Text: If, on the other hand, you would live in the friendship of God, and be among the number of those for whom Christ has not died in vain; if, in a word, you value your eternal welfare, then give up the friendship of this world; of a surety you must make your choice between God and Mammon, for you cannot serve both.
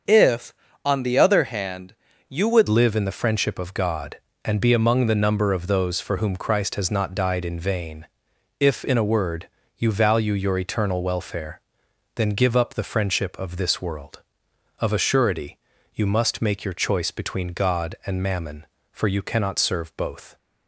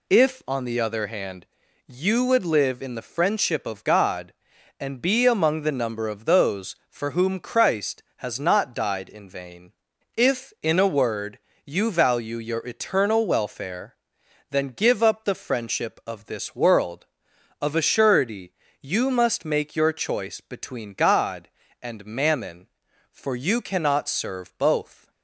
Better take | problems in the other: second | starts louder than the rest; until 1.4 s; 6.5 dB // changes voice at "live"; from 2.6 s on; 17.7 s long // pauses between "surety" and "you"; at 15.5 s; 0.38 s long; slight in the second

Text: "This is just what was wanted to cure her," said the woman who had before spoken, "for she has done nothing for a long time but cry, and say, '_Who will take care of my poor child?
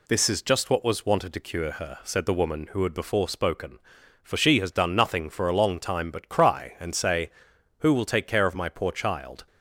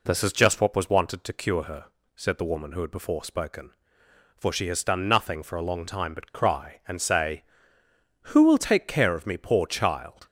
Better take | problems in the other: first | says "me" for "my"; at 9.2 s

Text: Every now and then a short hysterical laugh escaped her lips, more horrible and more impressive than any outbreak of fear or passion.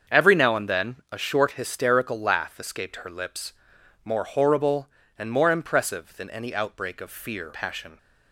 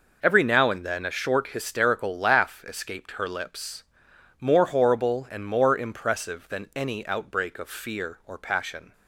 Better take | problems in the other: second | starts louder than the rest; until 1.2 s; 7 dB // skips "or"; at 7.5 s

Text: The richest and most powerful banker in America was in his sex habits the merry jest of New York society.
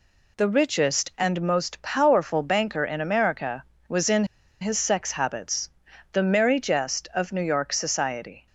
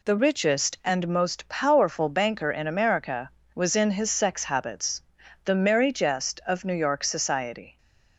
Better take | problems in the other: second | pauses between "in" and "his"; at 4.2 s; 0.37 s long // pauses between "habits" and "the"; at 5.7 s; 0.42 s long; also in the second

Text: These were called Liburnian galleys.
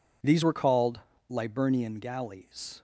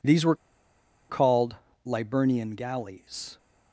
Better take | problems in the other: first | pauses between "were" and "called"; noticeable; at 0.3 s; 0.74 s long // pauses between "called" and "Liburnian"; slight; at 1.5 s; 0.30 s long; slight in the first

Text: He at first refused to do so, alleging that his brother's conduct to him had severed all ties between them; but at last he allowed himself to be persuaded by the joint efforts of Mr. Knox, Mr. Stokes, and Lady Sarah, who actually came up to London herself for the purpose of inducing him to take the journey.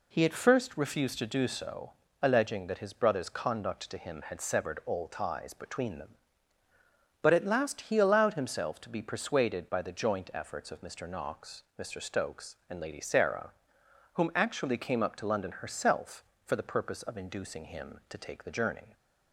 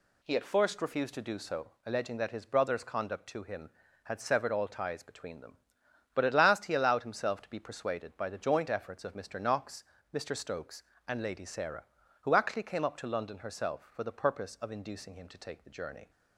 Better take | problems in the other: second | says "whom" for "who"; at 14.1 s

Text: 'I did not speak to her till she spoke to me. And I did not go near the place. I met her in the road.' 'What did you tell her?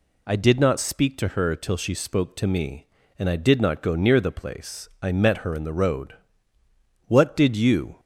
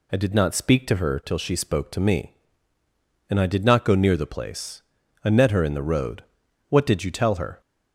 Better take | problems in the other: second | stops before "tell her"; at 7.9 s

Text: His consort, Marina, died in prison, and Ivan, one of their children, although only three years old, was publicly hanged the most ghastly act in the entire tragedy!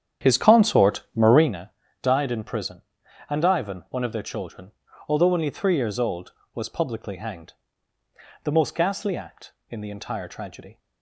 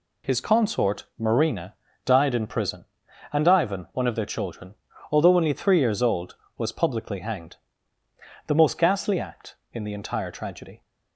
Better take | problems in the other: second | starts louder than the rest; strong; until 1.6 s; 9.5 dB // pauses between "hanged" and "the"; noticeable; at 7.5 s; 0.90 s long; noticeable in the second

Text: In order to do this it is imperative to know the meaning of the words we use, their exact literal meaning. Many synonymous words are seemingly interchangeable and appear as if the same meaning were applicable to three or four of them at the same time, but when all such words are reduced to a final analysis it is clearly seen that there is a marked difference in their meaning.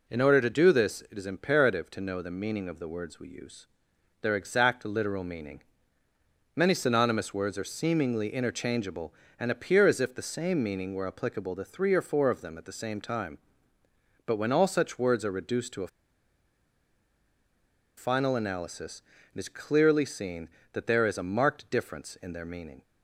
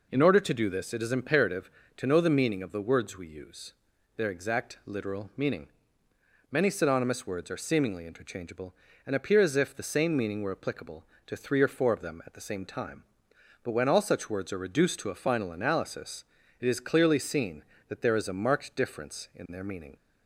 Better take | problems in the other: second | pauses between "a" and "final"; strong; at 15.8 s; 2.1 s long // pauses between "analysis" and "it"; slight; at 19.0 s; 0.32 s long; slight in the second

